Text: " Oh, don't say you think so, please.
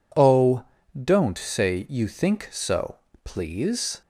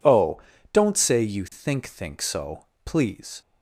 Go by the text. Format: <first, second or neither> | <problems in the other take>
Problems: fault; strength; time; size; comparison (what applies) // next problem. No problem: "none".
first | says "think" twice; at 1.8 s